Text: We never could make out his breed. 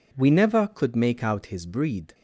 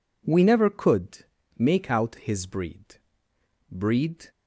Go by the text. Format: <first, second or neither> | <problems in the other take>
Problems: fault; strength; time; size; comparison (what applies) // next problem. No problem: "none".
first | pauses between "could" and "make"; slight; at 1.2 s; 0.34 s long // says "breed" twice; at 3.7 s